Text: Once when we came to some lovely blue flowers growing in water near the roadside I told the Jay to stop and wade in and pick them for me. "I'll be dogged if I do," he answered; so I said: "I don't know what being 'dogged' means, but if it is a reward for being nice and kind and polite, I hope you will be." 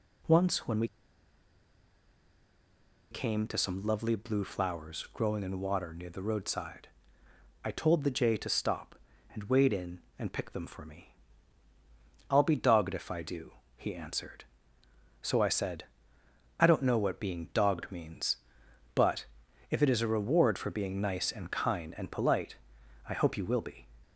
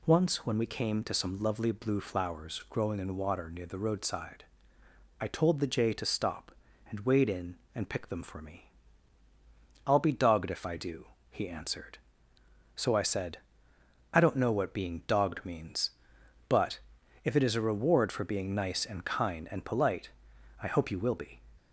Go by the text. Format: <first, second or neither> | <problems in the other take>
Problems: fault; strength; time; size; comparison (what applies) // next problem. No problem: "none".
second | pauses between "we" and "came"; strong; at 0.8 s; 2.2 s long // pauses between "roadside" and "I"; noticeable; at 6.8 s; 0.76 s long; noticeable in the second // pauses between "but" and "if"; noticeable; at 19.2 s; 0.46 s long; noticeable in the second